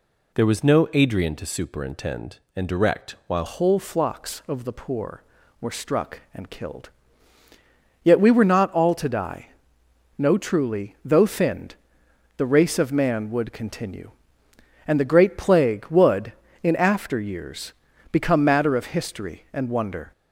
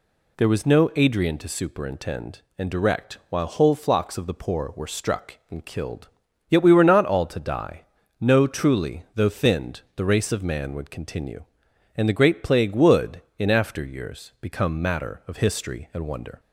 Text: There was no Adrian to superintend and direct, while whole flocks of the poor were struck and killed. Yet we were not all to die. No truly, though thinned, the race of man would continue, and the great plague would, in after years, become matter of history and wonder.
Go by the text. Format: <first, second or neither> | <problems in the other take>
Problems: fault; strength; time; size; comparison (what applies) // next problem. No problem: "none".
second | changes voice at "whole"; from 3.4 s on; 16.7 s long